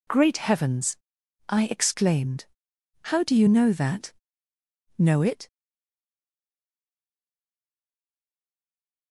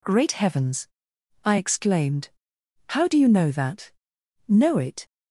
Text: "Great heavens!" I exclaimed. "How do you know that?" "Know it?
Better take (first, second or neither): second